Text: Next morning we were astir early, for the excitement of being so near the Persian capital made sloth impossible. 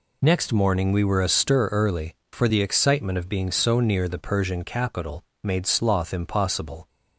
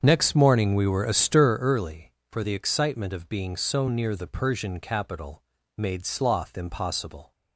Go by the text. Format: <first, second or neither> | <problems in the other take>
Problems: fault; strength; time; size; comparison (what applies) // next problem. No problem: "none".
first | starts louder than the rest; strong; until 1.6 s; 7 dB // pauses between "capital" and "made"; slight; at 5.4 s; 0.34 s long; slight in the first